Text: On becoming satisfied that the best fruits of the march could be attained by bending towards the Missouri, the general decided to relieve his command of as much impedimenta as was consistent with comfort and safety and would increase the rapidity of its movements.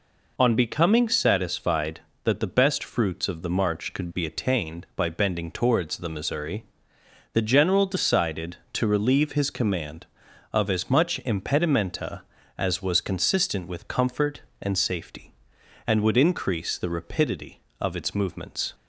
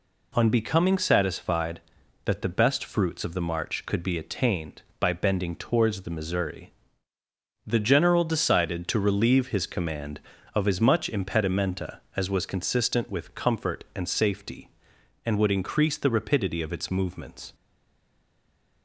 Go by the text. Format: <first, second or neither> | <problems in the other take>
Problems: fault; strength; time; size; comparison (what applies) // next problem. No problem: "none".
first | stays silent after the last word; noticeable; from 17.5 s on; 1.3 s long